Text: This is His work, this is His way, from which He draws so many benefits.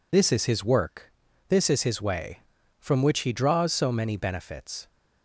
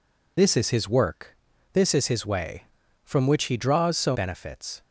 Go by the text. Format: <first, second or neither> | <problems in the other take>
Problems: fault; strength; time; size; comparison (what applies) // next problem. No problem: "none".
first | skips "many"; at 4.1 s